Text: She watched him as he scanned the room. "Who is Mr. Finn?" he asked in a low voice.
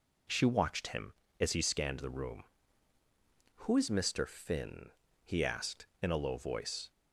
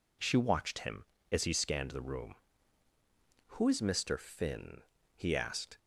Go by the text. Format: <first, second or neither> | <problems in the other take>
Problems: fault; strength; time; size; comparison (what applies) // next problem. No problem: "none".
first | stops before "in a low voice"; at 5.7 s